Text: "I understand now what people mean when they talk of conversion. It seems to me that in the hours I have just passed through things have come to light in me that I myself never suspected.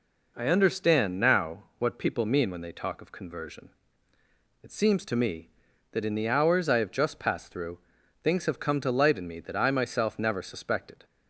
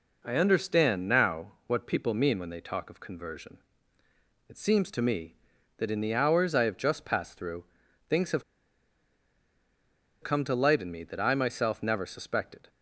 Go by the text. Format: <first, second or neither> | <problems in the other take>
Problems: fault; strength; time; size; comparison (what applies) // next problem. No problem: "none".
first | pauses between "through" and "things"; at 7.6 s; 0.44 s long; also in the first // pauses between "have" and "come"; strong; at 8.4 s; 1.7 s long